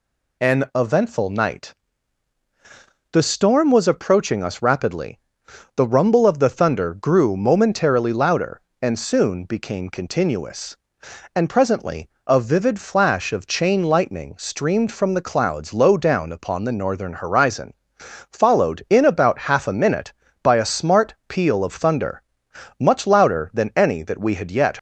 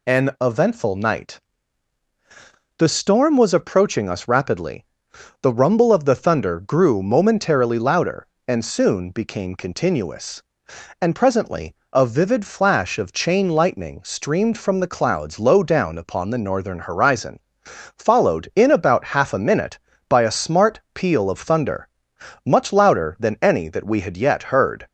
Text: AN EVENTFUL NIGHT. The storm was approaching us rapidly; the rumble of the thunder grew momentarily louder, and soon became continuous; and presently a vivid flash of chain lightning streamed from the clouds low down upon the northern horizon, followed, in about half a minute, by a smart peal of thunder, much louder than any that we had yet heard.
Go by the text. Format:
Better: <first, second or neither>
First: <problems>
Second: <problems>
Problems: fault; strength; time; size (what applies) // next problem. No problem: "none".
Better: second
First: pauses between "presently" and "a"; slight; at 12.0 s; 0.18 s long // stops before "heard"; at 24.7 s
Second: pauses between "presently" and "a"; slight; at 11.7 s; 0.18 s long